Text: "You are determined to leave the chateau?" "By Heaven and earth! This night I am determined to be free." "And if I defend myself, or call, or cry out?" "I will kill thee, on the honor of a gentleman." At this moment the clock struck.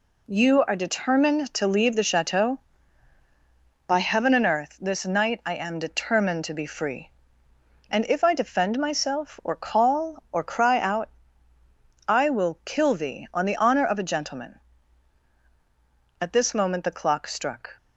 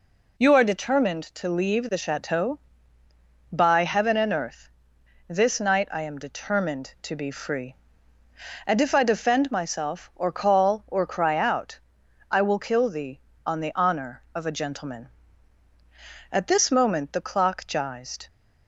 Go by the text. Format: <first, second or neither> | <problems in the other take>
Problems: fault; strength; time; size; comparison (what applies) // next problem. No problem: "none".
first | says "gized" for "struck"; at 17.6 s